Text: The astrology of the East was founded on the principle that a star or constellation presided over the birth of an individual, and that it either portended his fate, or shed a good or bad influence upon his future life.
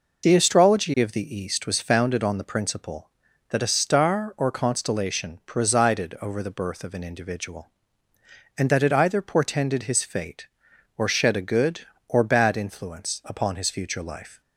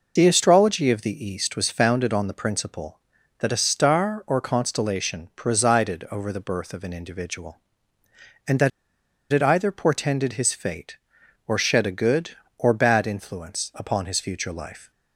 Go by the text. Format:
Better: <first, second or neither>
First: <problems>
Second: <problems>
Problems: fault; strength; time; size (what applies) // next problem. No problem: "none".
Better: first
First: none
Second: pauses between "that" and "it"; noticeable; at 8.6 s; 0.62 s long